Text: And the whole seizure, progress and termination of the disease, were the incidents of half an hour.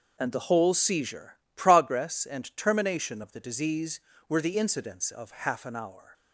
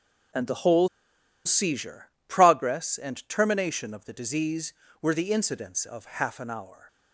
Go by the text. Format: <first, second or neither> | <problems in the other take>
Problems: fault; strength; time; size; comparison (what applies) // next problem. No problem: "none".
first | pauses between "whole" and "seizure"; noticeable; at 0.8 s; 0.57 s long